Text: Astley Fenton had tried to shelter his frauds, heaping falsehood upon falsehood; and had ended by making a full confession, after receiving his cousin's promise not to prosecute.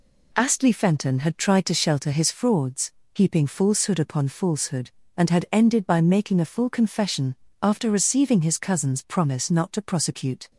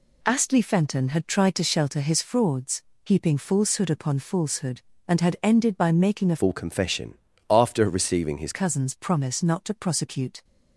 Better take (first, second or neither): first